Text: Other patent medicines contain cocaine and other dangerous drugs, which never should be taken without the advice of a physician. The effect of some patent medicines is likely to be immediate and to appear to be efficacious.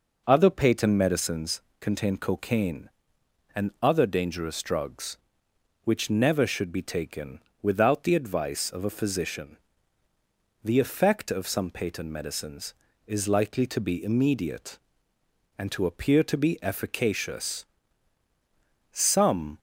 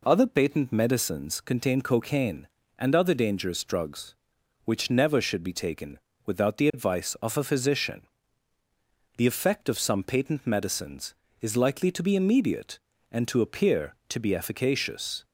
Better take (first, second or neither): second